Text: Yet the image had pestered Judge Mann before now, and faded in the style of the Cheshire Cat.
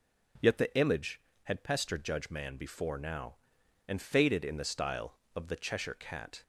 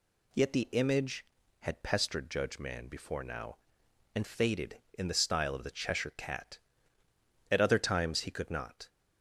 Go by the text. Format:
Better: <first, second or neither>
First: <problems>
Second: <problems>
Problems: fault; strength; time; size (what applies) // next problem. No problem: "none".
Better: first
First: none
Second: goes on to say "At other times he could not"; from 7.5 s on; 1.3 s long